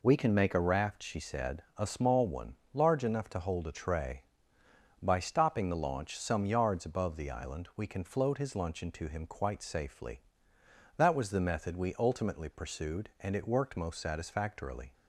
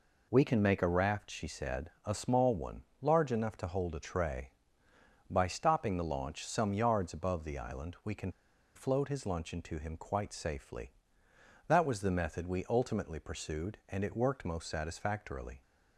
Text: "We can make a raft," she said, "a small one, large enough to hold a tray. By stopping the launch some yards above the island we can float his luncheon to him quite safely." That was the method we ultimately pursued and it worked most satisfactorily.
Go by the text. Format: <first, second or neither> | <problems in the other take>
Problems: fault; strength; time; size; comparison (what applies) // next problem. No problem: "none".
first | pauses between "can" and "float"; at 8.3 s; 0.44 s long